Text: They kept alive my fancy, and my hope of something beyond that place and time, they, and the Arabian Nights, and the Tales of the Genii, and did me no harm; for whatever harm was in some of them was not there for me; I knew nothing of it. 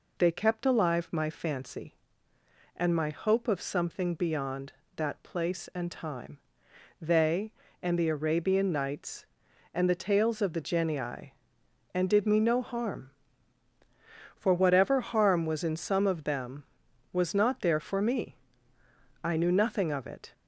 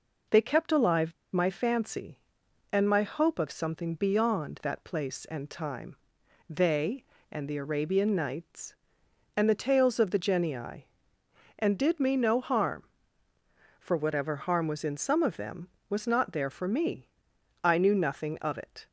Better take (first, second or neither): first